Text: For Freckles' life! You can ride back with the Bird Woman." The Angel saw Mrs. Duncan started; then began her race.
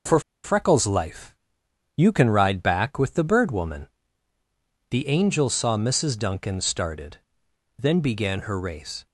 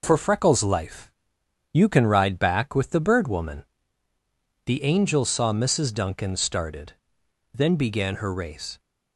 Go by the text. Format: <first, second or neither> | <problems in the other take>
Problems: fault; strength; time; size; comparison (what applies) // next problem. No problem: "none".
second | pauses between "For" and "Freckles"; slight; at 0.2 s; 0.23 s long